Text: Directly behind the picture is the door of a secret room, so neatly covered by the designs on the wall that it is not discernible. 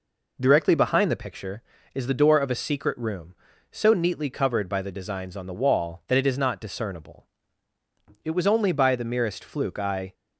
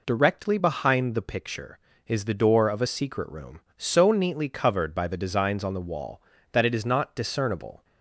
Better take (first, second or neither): second